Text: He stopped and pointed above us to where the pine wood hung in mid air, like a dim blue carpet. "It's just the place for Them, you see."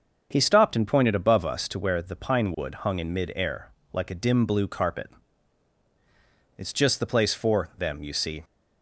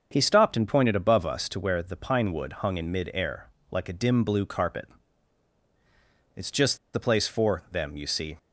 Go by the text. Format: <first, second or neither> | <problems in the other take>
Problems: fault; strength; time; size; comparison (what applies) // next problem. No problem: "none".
first | starts louder than the rest; until 1.1 s; 6.5 dB; also in the first // pauses between "just" and "the"; slight; at 6.7 s; 0.17 s long